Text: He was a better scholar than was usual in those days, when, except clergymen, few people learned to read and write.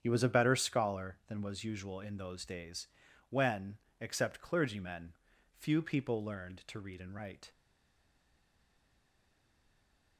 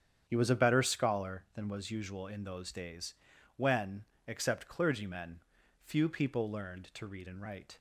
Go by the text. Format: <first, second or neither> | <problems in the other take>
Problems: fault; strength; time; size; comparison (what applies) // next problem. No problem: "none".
second | starts louder than the rest; strong; until 1.0 s; 8.5 dB; strong in the second // stays silent after the last word; strong; from 7.5 s on; 2.6 s long